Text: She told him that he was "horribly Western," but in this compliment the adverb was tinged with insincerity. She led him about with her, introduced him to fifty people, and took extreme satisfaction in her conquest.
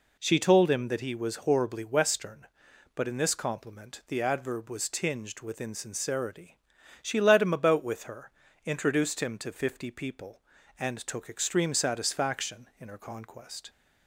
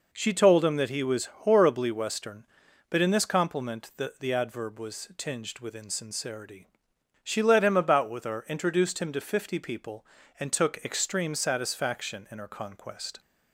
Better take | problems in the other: first | says "the" twice; at 4.1 s

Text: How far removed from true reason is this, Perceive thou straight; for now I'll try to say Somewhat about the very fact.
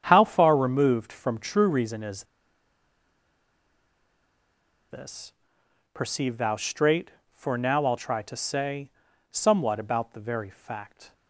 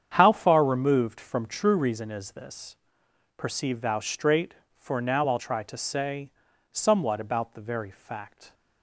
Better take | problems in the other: second | starts louder than the rest; strong; until 1.0 s; 8 dB; strong in the second // pauses between "is" and "this"; strong; at 2.2 s; 2.6 s long // pauses between "say" and "Somewhat"; at 8.9 s; 0.40 s long; also in the second

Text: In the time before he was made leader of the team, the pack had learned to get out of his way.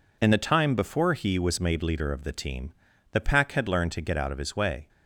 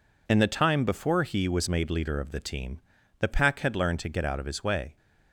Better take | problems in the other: neither | none

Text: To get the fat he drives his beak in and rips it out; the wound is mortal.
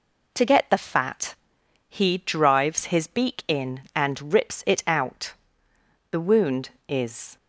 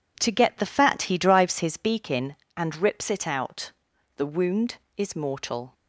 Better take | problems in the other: second | pauses between "fat" and "he"; noticeable; at 1.3 s; 0.54 s long // stops before "mortal"; at 7.3 s

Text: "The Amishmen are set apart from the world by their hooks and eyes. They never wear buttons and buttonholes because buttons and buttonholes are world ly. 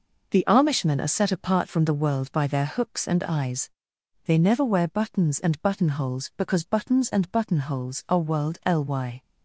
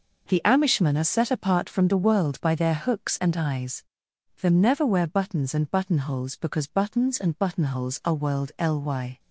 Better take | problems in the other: first | says "Them" for "They"; at 4.4 s

